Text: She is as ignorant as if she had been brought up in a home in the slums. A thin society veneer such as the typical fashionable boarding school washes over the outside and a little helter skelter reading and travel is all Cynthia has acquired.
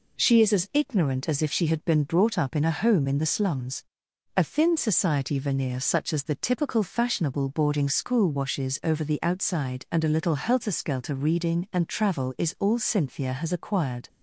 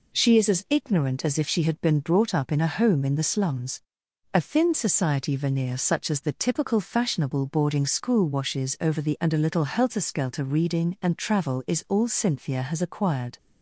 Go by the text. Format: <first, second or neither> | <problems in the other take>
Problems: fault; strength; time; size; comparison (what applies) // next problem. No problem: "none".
first | skips "outside"; at 9.1 s